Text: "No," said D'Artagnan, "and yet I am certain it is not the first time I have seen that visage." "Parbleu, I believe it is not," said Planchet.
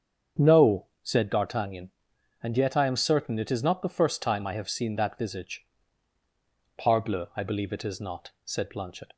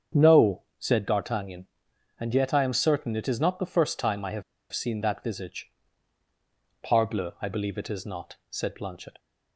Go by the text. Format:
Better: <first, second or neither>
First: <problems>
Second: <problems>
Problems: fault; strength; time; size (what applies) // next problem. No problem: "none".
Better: first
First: starts louder than the rest; strong; until 1.5 s; 7.5 dB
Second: starts louder than the rest; strong; until 1.3 s; 7.5 dB // pauses between "have" and "seen"; slight; at 4.4 s; 0.29 s long